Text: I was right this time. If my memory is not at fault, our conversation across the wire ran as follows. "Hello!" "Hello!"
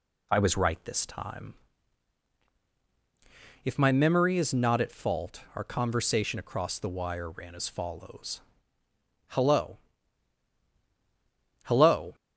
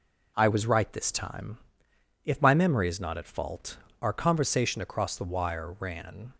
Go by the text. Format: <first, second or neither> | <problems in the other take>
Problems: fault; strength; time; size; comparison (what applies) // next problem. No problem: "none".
first | stops before "as follows Hello Hello"; at 6.3 s